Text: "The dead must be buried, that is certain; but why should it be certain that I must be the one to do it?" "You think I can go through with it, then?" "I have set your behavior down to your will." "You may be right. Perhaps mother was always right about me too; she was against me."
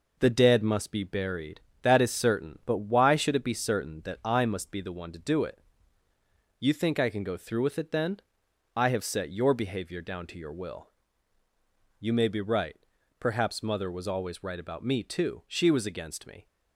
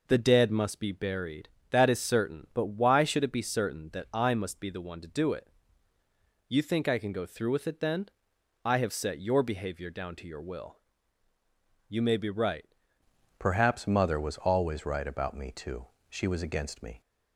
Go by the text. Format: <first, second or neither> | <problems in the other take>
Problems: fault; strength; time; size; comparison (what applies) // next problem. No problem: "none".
first | changes voice at "Perhaps"; from 13.3 s on; 3.7 s long